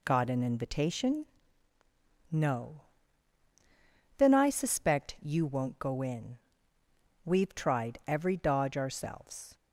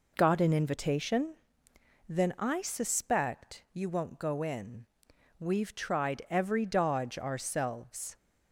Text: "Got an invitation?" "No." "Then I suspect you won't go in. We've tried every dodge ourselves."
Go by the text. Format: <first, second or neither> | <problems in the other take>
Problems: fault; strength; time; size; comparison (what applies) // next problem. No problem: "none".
first | skips "No"; at 1.7 s